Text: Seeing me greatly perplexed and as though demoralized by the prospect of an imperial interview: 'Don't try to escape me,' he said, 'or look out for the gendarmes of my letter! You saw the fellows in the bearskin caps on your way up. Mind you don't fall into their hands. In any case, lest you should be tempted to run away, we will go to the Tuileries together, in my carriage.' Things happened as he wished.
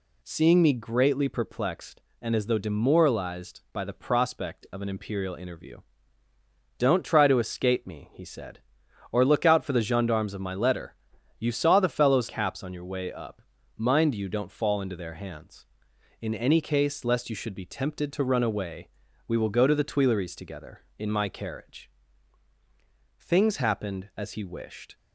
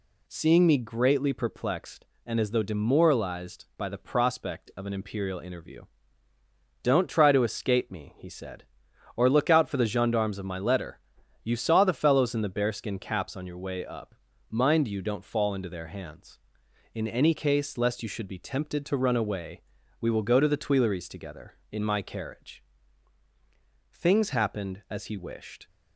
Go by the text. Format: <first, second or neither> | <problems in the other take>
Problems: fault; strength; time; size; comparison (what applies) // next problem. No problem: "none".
second | skips "in the bearskin"; at 12.2 s